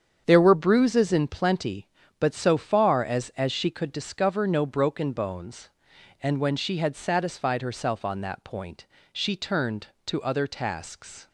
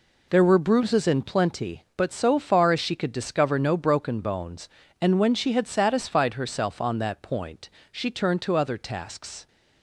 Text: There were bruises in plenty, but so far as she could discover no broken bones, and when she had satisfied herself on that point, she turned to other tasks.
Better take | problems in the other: second | starts louder than the rest; strong; until 1.2 s; 7.5 dB // says "as" twice; at 3.3 s

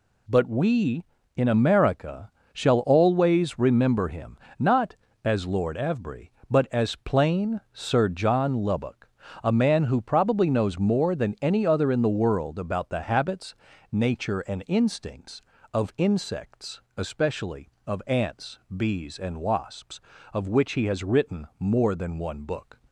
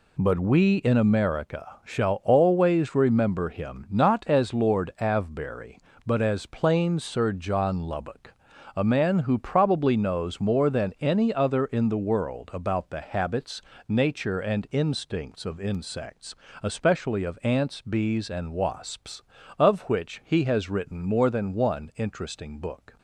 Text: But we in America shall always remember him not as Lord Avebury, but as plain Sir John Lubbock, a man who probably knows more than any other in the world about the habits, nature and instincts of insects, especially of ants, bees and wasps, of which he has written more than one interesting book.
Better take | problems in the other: second | pauses between "America" and "shall"; slight; at 2.3 s; 0.22 s long // pauses between "him" and "not"; slight; at 4.3 s; 0.20 s long // skips "interesting"; at 22.4 s

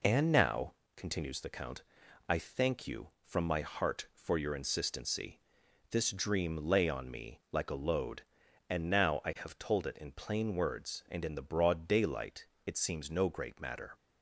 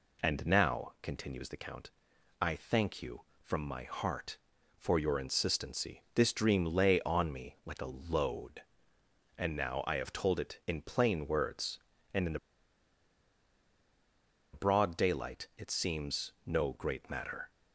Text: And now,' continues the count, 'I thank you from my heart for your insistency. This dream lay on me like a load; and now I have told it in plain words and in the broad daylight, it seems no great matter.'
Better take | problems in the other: first | pauses between "the" and "broad"; strong; at 12.3 s; 2.1 s long

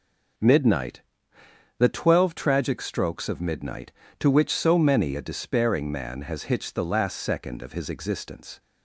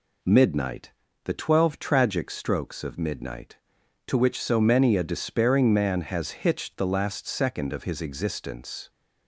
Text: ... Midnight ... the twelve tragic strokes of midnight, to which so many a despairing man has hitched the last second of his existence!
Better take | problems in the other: neither | none

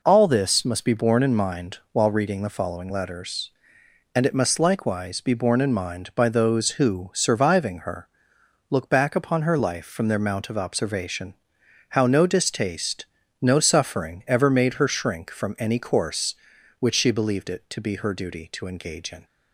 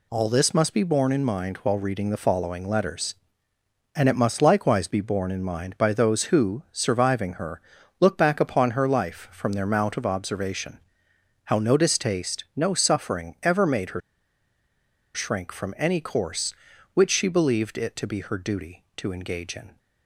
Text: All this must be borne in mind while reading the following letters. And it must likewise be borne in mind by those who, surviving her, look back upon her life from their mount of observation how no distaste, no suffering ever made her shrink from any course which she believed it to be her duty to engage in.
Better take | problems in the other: first | pauses between "observation" and "how"; noticeable; at 10.7 s; 0.70 s long; noticeable in the first // pauses between "her" and "shrink"; at 14.0 s; 1.1 s long

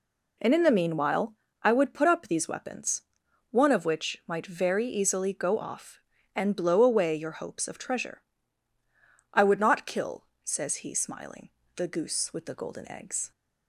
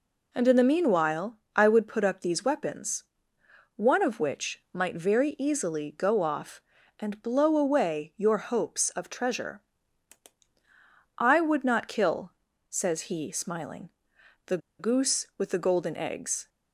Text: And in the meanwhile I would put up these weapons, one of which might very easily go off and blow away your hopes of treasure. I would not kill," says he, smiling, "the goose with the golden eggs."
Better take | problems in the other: first | pauses between "meanwhile" and "I"; slight; at 1.3 s; 0.18 s long; slight in the first // pauses between "the" and "goose"; slight; at 14.5 s; 0.21 s long

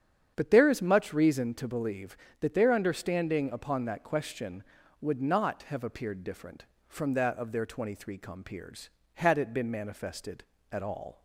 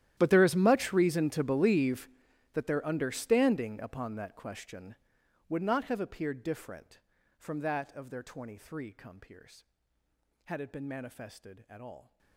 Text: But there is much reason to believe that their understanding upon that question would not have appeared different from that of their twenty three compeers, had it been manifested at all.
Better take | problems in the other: first | gets quieter; strong; throughout; 23 dB // starts louder than the rest; strong; until 1.1 s; 12 dB; strong in the first

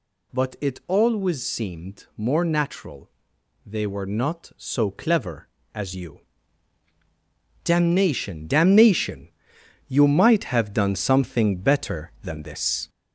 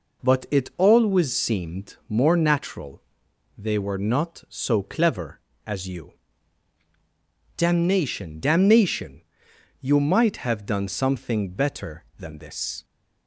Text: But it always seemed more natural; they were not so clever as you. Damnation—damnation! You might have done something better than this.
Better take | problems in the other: second | gets louder; noticeable; throughout; 4.5 dB

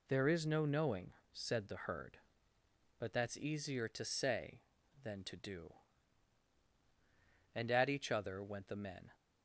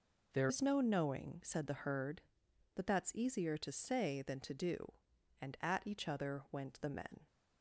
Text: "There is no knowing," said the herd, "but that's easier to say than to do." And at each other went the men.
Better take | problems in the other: first | changes voice at "is"; from 0.4 s on; 6.8 s long

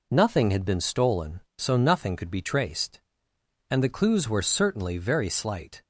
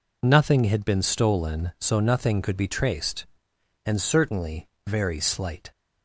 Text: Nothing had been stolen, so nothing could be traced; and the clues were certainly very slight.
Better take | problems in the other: first | skips "the clues were"; at 4.0 s // pauses between "certainly" and "very"; slight; at 4.6 s; 0.18 s long

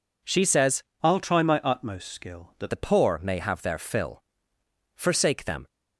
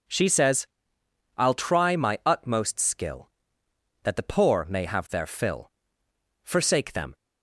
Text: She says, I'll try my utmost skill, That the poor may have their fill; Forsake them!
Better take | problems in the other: second | changes voice from "I'll" to "That"; from 1.0 to 2.6 s; 1.6 s long

